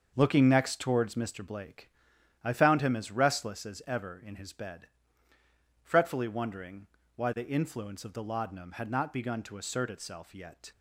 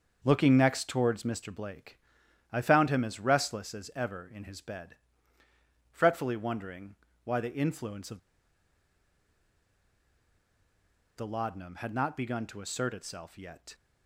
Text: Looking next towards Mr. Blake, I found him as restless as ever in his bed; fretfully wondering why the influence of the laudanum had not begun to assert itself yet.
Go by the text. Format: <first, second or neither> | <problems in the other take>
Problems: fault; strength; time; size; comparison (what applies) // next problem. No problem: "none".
first | starts louder than the rest; until 1.2 s; 6.5 dB; also in the first // pauses between "wondering" and "why"; slight; at 6.9 s; 0.30 s long; slight in the first // pauses between "of" and "the"; strong; at 8.1 s; 2.9 s long